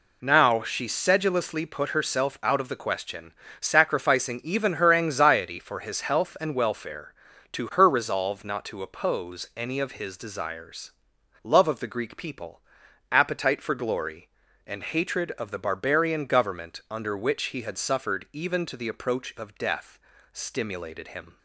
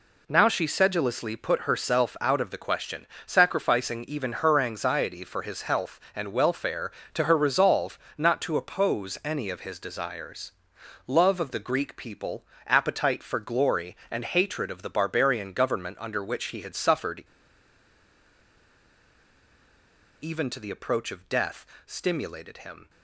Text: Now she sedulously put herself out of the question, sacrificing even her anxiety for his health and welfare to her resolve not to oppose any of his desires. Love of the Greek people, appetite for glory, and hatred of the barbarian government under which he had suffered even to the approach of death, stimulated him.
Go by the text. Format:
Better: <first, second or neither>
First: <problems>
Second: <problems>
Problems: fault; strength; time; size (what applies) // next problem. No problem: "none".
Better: first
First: none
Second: pauses between "resolve" and "not"; slight; at 7.9 s; 0.18 s long // pauses between "suffered" and "even"; strong; at 17.2 s; 2.9 s long